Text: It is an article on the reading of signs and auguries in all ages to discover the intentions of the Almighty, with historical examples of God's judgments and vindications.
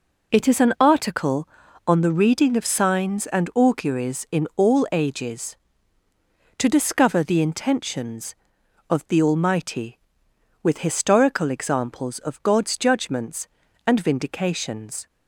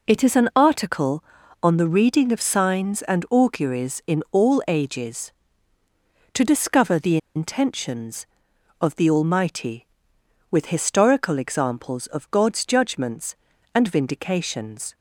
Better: first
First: none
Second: pauses between "the" and "intentions"; slight; at 7.1 s; 0.18 s long

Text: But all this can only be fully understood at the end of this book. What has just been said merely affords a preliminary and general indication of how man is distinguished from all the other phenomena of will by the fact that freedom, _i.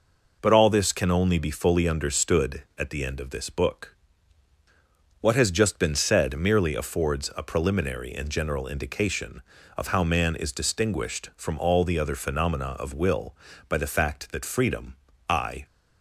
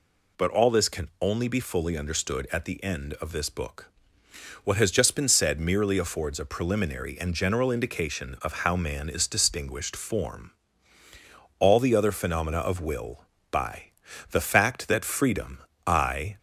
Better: first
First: none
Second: says "form" for "from"; at 9.9 s // pauses between "by" and "the"; at 13.9 s; 0.40 s long

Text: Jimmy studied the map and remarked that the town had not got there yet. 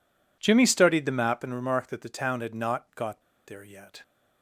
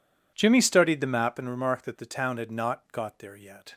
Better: second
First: pauses between "got" and "there"; slight; at 3.2 s; 0.24 s long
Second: none

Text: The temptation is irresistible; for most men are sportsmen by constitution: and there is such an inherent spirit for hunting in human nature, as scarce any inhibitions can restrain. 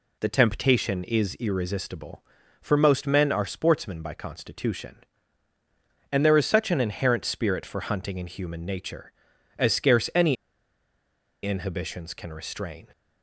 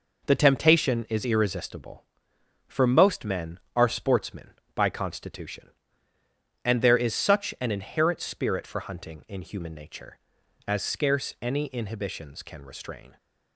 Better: second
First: pauses between "any" and "inhibitions"; at 10.3 s; 1.0 s long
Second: none

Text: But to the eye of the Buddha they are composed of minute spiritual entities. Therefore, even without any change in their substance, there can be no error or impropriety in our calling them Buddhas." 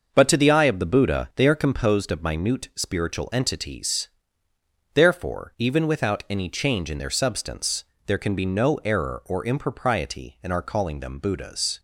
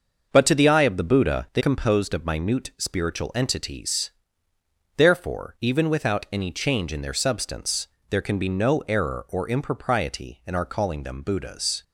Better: first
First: starts louder than the rest; until 1.1 s; 6 dB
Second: starts louder than the rest; until 1.3 s; 6 dB // skips "are"; at 1.6 s

